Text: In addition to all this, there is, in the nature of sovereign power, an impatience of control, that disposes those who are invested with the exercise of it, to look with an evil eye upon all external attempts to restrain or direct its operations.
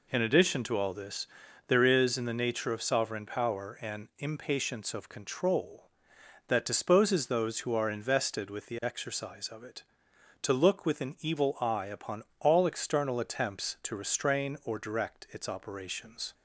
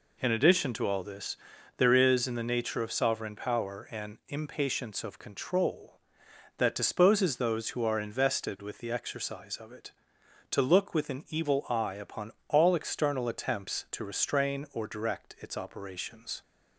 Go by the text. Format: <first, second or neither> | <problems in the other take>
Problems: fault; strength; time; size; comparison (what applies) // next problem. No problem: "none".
neither | pauses between "upon" and "all"; slight; the same in both